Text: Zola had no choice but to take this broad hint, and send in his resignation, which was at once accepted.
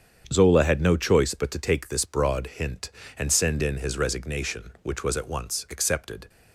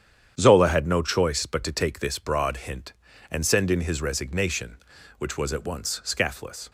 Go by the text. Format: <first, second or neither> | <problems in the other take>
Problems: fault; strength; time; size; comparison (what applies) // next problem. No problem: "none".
first | starts louder than the rest; strong; until 1.4 s; 9 dB; strong in the first // says "scathless" for "accepted"; at 6.0 s